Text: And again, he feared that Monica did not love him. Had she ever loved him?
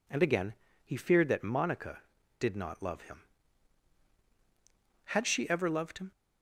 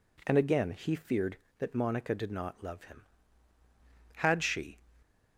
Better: first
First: none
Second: stops before "ever loved him"; at 5.0 s

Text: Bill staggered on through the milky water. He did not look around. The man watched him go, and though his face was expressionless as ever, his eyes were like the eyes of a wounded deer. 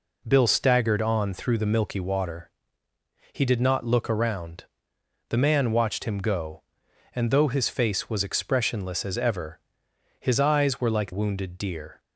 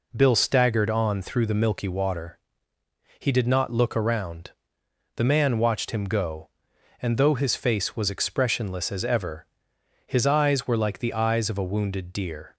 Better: second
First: skips "the eyes of a"; at 11.1 s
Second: none

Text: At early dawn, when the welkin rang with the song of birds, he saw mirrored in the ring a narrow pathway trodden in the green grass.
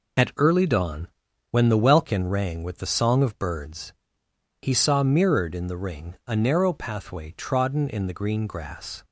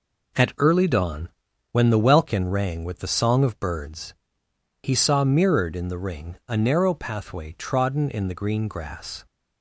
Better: second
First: loses the start of "At"; at 0.1 s; 30 ms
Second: none

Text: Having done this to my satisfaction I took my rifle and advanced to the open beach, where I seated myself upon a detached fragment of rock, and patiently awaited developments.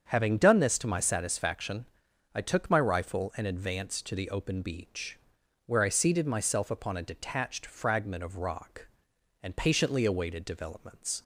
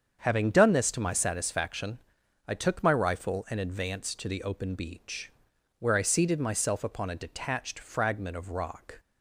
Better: first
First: starts louder than the rest; strong; until 1.1 s; 7 dB // pauses between "satisfaction" and "I"; noticeable; at 1.8 s; 0.48 s long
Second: starts louder than the rest; strong; until 1.2 s; 7.5 dB // pauses between "satisfaction" and "I"; noticeable; at 1.9 s; 0.48 s long // stops before "and patiently awaited developments"; at 8.9 s

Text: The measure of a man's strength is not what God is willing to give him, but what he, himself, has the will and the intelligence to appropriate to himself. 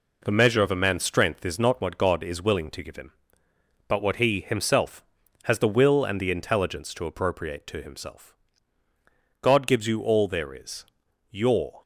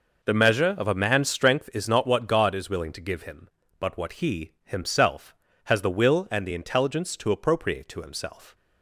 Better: second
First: goes on to say "God gives you all there is your"; strong; from 9.4 s on; 2.4 s long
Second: none

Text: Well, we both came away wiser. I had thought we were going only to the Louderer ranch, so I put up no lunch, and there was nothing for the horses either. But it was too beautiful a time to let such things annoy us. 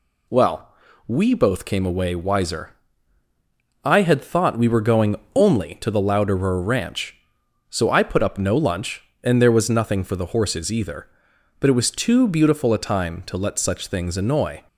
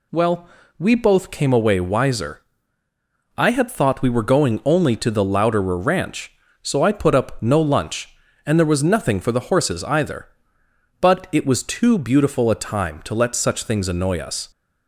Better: second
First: pauses between "going" and "only"; slight; at 5.1 s; 0.20 s long // stops before "us"; at 14.6 s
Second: none

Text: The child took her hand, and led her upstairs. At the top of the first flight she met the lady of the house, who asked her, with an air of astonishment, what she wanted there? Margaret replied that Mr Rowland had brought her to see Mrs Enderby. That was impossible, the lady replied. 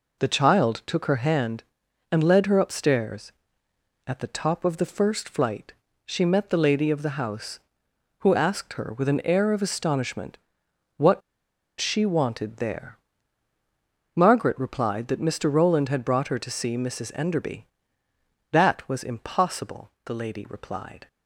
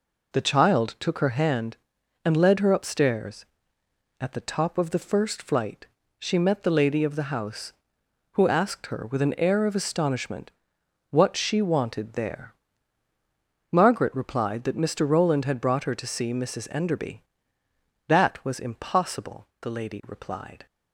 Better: second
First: pauses between "flight" and "she"; slight; at 5.7 s; 0.34 s long // pauses between "what" and "she"; noticeable; at 11.2 s; 0.58 s long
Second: pauses between "flight" and "she"; slight; at 5.8 s; 0.34 s long

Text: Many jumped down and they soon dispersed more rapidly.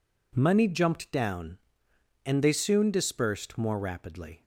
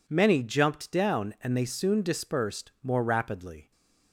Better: second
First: says "Money" for "Many"; at 0.3 s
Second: none

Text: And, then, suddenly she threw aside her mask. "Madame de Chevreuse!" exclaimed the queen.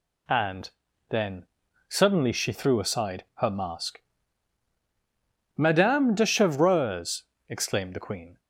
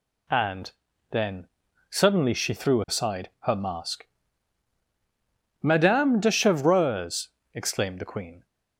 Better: neither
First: none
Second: none

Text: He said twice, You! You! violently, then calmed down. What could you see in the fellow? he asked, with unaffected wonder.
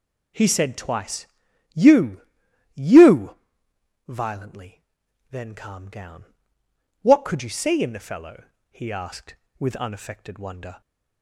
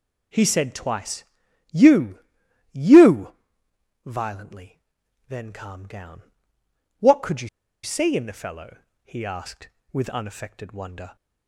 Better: first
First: none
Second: pauses between "you" and "see"; slight; at 7.4 s; 0.34 s long

